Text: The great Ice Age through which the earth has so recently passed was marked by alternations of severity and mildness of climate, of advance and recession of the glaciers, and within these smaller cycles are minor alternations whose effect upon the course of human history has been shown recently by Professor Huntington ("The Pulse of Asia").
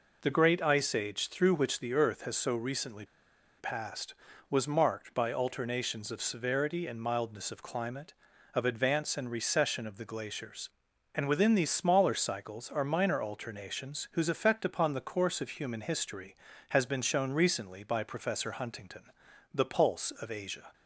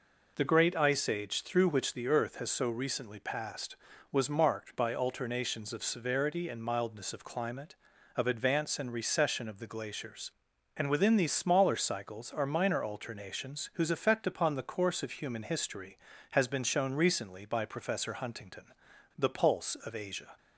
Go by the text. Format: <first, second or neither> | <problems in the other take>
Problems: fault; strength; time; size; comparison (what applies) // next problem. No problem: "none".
second | pauses between "recently" and "passed"; noticeable; at 3.0 s; 0.54 s long